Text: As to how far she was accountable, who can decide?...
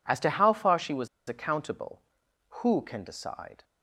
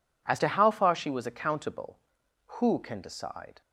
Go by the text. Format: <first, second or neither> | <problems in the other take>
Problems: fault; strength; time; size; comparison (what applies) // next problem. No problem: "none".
second | pauses between "was" and "accountable"; slight; at 1.0 s; 0.19 s long